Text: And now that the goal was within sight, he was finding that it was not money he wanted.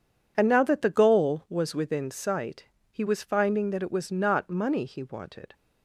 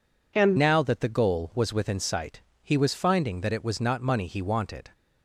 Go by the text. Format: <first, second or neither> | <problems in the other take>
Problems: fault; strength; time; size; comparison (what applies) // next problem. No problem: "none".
first | changes voice at "now"; from 0.5 s on; 4.3 s long